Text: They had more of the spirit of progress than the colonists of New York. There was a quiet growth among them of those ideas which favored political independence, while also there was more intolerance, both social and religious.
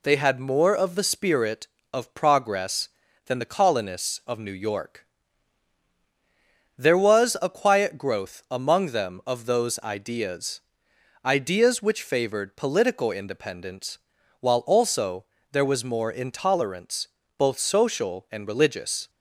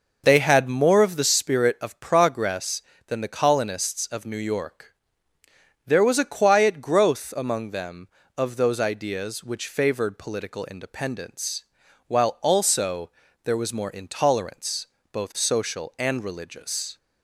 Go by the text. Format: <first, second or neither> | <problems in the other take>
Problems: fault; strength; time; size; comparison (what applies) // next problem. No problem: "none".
second | says "ideas" twice; at 11.2 s // pauses between "also" and "there"; slight; at 15.2 s; 0.26 s long; slight in the second